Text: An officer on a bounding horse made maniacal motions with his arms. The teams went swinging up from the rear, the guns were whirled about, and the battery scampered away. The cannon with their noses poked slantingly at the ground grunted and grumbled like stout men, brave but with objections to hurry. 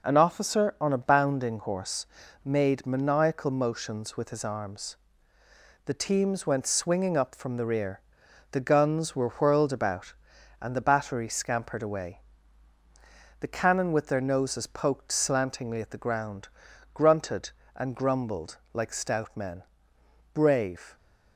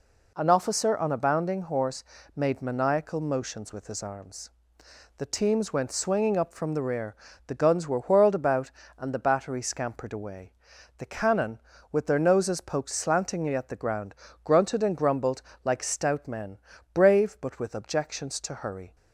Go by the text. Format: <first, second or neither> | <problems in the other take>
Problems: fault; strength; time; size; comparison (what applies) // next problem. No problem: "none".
second | pauses between "horse" and "made"; at 2.0 s; 0.38 s long; slight in the second // pauses between "ground" and "grunted"; noticeable; at 16.4 s; 0.46 s long; slight in the second // pauses between "grumbled" and "like"; slight; at 18.5 s; 0.18 s long; slight in the second // stops before "but with objections to hurry"; at 20.9 s